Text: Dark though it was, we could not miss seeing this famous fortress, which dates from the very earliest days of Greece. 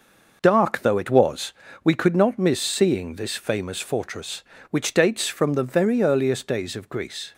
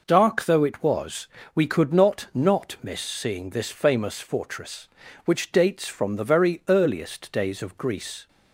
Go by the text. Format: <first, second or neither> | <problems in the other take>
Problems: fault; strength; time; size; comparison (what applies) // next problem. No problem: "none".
first | says "not" twice; at 2.3 s